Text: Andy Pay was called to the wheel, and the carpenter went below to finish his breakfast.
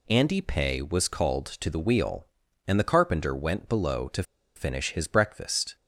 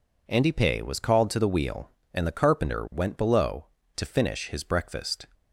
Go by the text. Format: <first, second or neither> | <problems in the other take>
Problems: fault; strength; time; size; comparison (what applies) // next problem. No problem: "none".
second | pauses between "to" and "finish"; slight; at 4.2 s; 0.33 s long